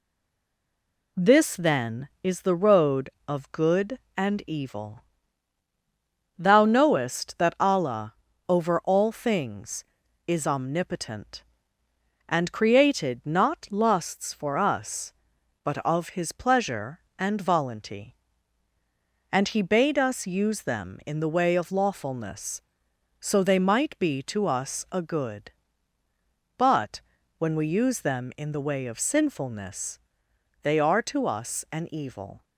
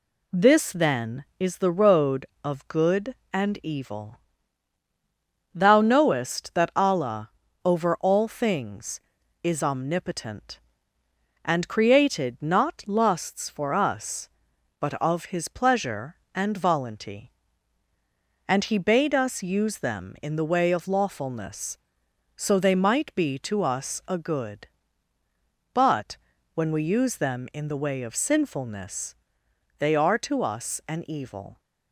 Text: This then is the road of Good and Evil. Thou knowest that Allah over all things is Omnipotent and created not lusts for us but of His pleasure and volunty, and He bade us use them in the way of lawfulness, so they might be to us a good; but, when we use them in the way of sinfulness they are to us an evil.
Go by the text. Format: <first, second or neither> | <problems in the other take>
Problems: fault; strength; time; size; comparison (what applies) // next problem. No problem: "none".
second | stays silent before the first word; until 1.1 s; 1.1 s long // pauses between "Allah" and "over"; slight; at 8.1 s; 0.34 s long; slight in the second // pauses between "sinfulness" and "they"; noticeable; at 30.0 s; 0.62 s long; noticeable in the second